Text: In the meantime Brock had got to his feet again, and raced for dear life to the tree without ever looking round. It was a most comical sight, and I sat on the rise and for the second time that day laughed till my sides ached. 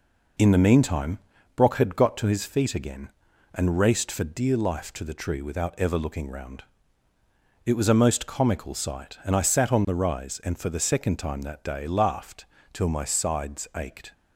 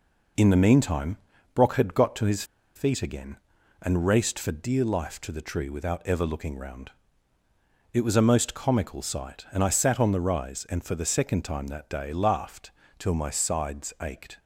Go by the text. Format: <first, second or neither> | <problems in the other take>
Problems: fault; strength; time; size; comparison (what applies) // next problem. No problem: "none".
first | pauses between "meantime" and "Brock"; slight; at 1.1 s; 0.36 s long; slight in the first // pauses between "his" and "feet"; slight; at 2.4 s; 0.32 s long // pauses between "laughed" and "till"; slight; at 12.7 s; 0.26 s long; slight in the first